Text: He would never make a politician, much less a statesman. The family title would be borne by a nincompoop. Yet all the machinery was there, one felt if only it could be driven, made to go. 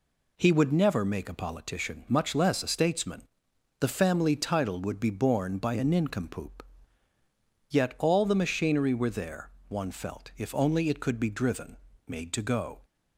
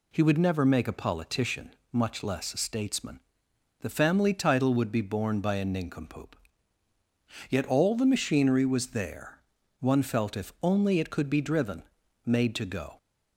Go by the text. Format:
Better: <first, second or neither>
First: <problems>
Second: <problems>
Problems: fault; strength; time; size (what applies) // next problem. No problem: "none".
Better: second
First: says "were" for "was"; at 8.9 s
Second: none